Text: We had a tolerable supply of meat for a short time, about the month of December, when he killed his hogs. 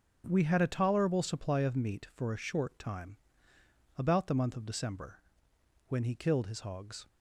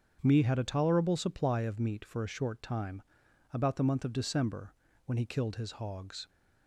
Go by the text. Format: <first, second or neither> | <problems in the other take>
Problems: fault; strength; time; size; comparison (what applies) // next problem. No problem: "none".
first | starts louder than the rest; strong; until 1.2 s; 7.5 dB; noticeable in the first // says "Me" for "We"; at 0.2 s